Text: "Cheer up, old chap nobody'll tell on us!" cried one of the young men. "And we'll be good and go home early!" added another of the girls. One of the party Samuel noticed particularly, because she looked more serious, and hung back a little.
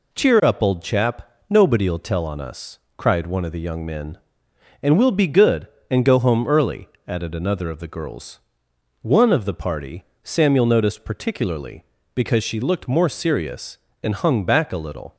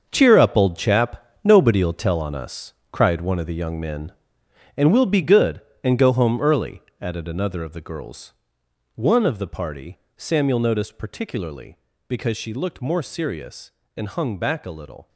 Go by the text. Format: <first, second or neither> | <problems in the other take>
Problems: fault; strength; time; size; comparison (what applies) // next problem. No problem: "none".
first | gets quieter; strong; throughout; 11 dB // pauses between "chap" and "nobody'll"; slight; at 1.2 s; 0.18 s long; slight in the first // pauses between "party" and "Samuel"; slight; at 9.9 s; 0.20 s long; slight in the first